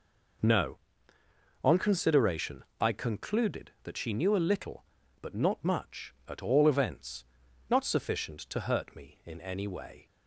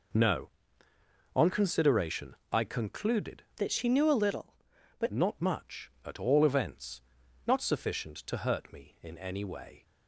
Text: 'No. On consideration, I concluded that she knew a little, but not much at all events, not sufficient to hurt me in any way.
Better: first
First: none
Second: changes voice from "that" to "but"; from 3.5 to 5.0 s; 1.5 s long

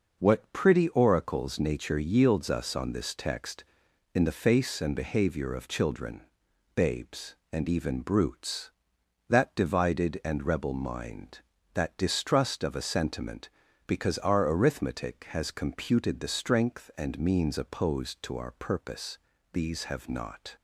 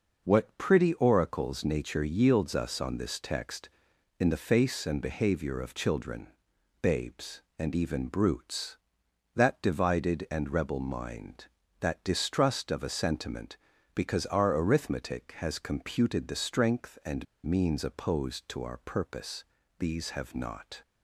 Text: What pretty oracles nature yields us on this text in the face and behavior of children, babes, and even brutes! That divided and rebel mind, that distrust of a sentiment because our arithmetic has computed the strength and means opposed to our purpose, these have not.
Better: first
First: none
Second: pauses between "and" and "means"; slight; at 17.2 s; 0.20 s long

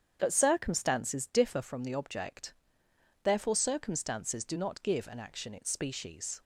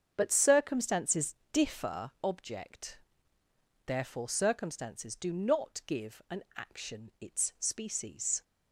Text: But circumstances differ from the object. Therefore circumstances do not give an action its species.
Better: first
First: starts louder than the rest; strong; until 1.2 s; 8 dB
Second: starts louder than the rest; strong; until 1.1 s; 7.5 dB // pauses between "circumstances" and "differ"; slight; at 1.3 s; 0.18 s long // skips "from the"; at 2.1 s

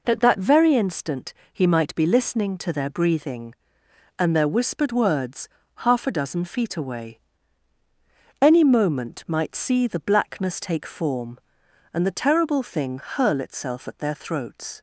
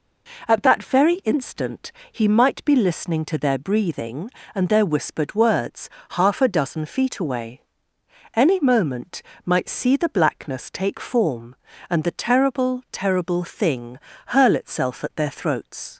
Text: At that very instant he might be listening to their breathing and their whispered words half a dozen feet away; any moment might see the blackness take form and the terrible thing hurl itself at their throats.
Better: first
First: pauses between "instant" and "he"; slight; at 1.3 s; 0.18 s long // pauses between "words" and "half"; slight; at 5.4 s; 0.30 s long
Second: pauses between "instant" and "he"; slight; at 1.9 s; 0.20 s long // pauses between "words" and "half"; slight; at 5.8 s; 0.22 s long // pauses between "moment" and "might"; slight; at 9.2 s; 0.22 s long // says "terrible" twice; at 12.9 s // pauses between "thing" and "hurl"; slight; at 13.9 s; 0.28 s long

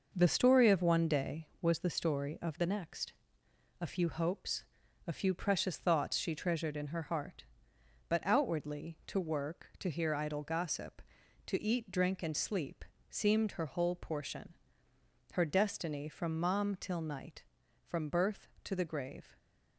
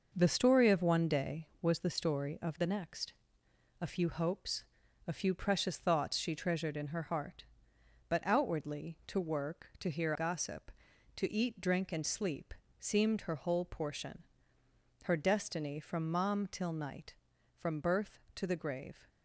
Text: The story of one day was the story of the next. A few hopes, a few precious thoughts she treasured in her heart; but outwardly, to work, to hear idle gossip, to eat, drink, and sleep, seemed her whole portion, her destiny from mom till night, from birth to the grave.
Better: first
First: none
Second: skips "idle"; at 10.1 s

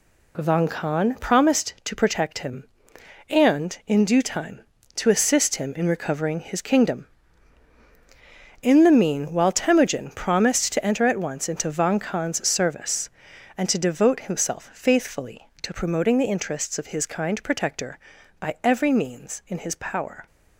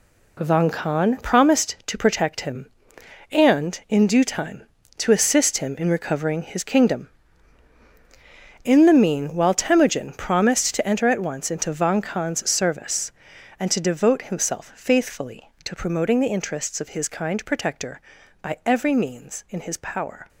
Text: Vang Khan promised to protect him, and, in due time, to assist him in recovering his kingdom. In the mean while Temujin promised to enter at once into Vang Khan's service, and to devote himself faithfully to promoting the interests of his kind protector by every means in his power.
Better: first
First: none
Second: gets quieter; strong; throughout; 8.5 dB

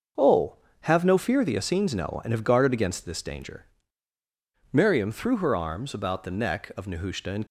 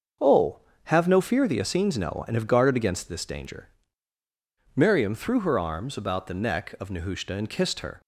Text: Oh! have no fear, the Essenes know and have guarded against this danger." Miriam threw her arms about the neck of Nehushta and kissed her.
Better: second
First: starts louder than the rest; until 1.4 s; 6.5 dB // stops before "kissed her"; at 7.4 s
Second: starts louder than the rest; until 1.4 s; 6.5 dB

